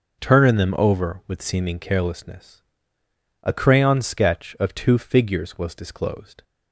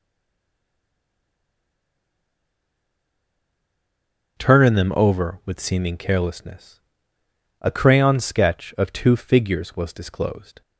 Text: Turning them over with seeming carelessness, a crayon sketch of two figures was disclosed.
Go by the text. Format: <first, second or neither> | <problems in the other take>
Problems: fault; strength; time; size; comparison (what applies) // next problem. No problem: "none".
first | stays silent before the first word; strong; until 4.3 s; 4.3 s long